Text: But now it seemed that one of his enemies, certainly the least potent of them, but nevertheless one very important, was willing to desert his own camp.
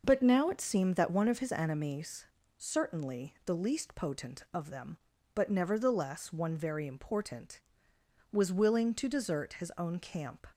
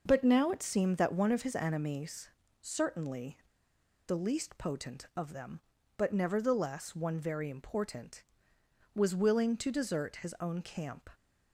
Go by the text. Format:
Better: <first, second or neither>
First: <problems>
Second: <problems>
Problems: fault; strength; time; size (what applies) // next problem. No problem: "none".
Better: first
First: none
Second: pauses between "certainly" and "the"; noticeable; at 3.3 s; 0.68 s long